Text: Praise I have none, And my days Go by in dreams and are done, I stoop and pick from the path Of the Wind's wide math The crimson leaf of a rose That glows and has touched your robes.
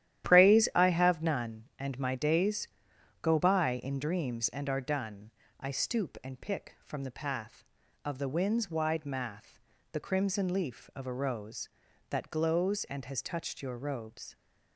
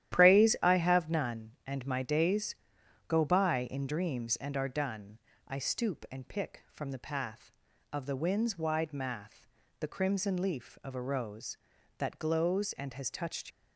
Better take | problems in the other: first | starts louder than the rest; strong; until 1.1 s; 11.5 dB; strong in the first // pauses between "days" and "Go"; noticeable; at 2.5 s; 0.54 s long; noticeable in the first // pauses between "math" and "The"; slight; at 9.4 s; 0.34 s long; slight in the first // stops before "your robes"; at 13.4 s

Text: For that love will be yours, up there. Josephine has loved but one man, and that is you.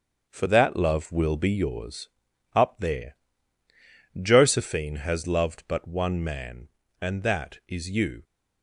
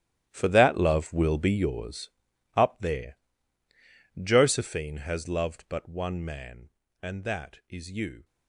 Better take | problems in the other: first | gets quieter; strong; throughout; 13 dB // starts louder than the rest; strong; until 1.3 s; 12 dB; also in the first

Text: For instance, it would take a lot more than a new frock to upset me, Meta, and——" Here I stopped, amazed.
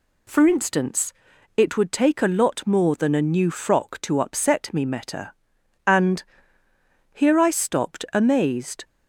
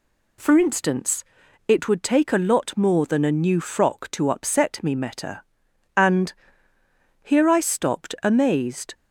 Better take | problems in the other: neither | none

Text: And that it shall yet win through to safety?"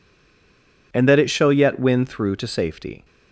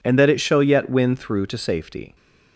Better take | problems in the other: second | stays silent before the first word; slight; until 0.9 s; 0.9 s long

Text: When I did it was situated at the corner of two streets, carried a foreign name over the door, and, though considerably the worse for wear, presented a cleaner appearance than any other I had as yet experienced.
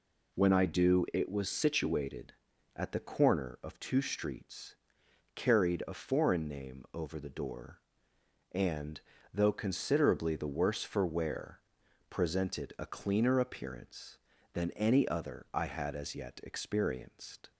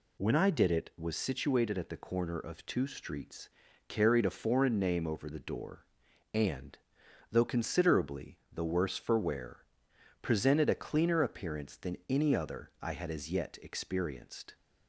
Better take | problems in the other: second | says "do" for "did"; at 0.6 s

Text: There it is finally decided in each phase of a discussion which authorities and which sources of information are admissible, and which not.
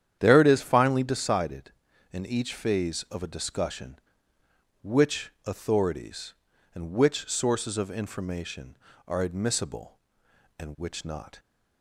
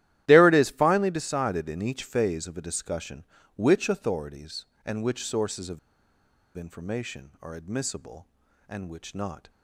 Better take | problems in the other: first | starts louder than the rest; strong; until 1.2 s; 13 dB; strong in the first // pauses between "of" and "information"; noticeable; at 5.7 s; 0.78 s long

